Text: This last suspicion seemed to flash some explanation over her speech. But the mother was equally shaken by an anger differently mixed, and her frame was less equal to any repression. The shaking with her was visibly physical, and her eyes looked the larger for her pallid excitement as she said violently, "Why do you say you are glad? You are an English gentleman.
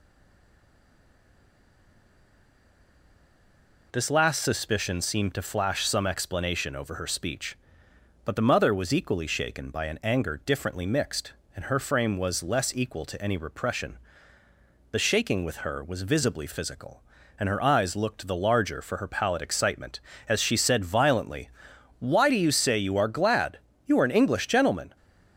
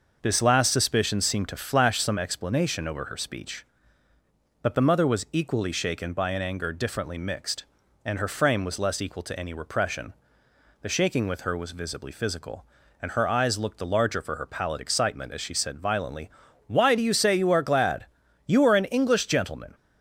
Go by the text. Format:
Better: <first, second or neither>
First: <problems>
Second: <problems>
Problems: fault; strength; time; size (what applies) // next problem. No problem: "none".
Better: second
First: stays silent before the first word; strong; until 3.9 s; 3.9 s long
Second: none